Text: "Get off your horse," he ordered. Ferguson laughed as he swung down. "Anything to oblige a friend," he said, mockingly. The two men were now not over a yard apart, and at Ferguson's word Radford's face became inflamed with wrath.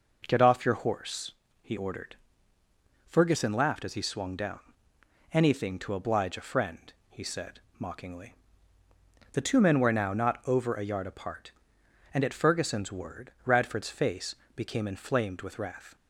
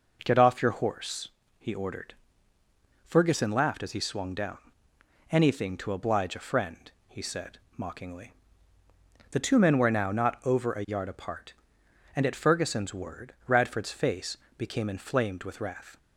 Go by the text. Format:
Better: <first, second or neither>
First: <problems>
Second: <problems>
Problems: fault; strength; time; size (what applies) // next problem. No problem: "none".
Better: neither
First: pauses between "face" and "became"; slight; at 14.3 s; 0.20 s long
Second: pauses between "face" and "became"; slight; at 14.3 s; 0.20 s long